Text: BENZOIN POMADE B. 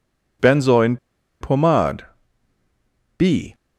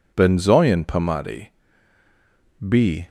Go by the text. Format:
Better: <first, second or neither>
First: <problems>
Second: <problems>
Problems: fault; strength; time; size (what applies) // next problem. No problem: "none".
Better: second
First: pauses between "BENZOIN" and "POMADE"; at 0.9 s; 0.44 s long // pauses between "POMADE" and "B"; at 2.0 s; 1.1 s long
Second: pauses between "POMADE" and "B"; at 1.5 s; 1.1 s long